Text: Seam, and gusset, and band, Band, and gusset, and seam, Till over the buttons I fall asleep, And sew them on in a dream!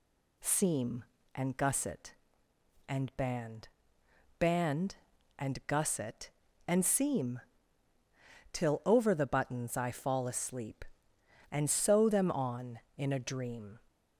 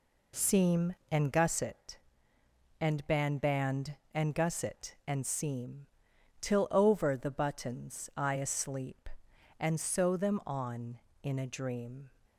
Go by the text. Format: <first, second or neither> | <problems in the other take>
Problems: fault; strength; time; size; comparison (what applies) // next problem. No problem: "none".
first | skips "fall"; at 8.3 s